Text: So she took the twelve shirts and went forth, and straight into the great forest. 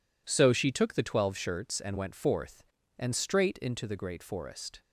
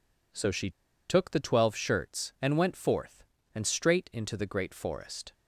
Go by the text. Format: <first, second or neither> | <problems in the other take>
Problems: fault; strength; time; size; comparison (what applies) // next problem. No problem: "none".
first | pauses between "she" and "took"; at 0.6 s; 0.37 s long